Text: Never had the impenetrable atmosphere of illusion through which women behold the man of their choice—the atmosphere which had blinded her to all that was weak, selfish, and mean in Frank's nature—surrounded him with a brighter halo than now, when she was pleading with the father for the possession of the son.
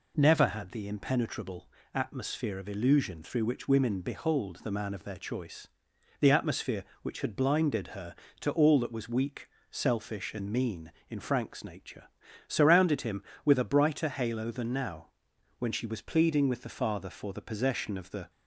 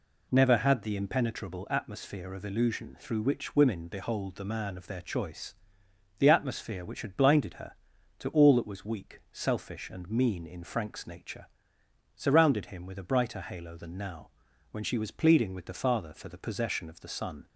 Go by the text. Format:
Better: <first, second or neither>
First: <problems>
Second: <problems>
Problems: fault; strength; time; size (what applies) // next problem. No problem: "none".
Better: second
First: pauses between "impenetrable" and "atmosphere"; slight; at 1.6 s; 0.26 s long // stops before "son"; at 18.2 s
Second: none